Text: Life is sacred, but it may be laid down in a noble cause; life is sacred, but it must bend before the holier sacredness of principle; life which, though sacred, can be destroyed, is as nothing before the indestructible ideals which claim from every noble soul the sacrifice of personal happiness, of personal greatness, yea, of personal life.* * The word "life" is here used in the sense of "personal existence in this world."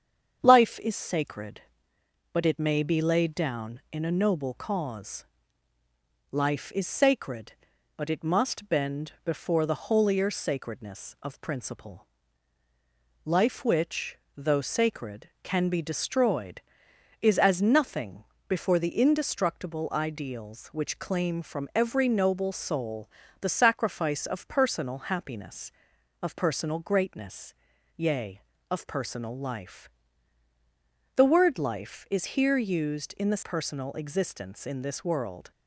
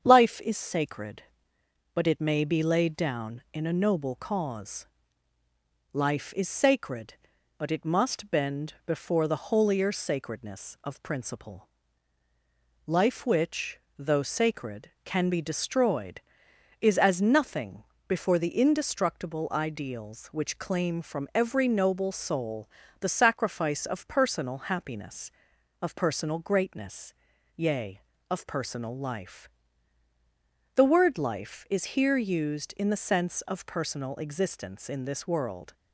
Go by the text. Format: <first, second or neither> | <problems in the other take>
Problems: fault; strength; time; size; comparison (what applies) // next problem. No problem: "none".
second | starts louder than the rest; strong; until 1.4 s; 7.5 dB; strong in the second // pauses between "nothing" and "before"; slight; at 18.2 s; 0.24 s long; slight in the second // pauses between "soul" and "the"; slight; at 23.0 s; 0.32 s long; slight in the second // skips "sense of"; at 33.4 s